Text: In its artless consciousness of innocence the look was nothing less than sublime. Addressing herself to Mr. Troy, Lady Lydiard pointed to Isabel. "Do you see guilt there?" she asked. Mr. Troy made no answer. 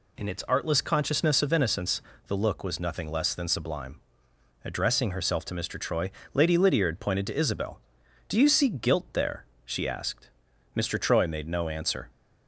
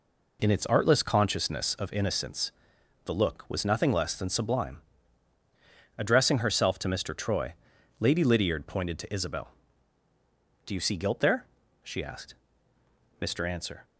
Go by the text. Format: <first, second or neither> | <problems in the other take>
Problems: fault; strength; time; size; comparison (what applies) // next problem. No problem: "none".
first | pauses between "innocence" and "the"; noticeable; at 2.5 s; 0.54 s long; slight in the first // skips "Troy made no"; at 13.4 s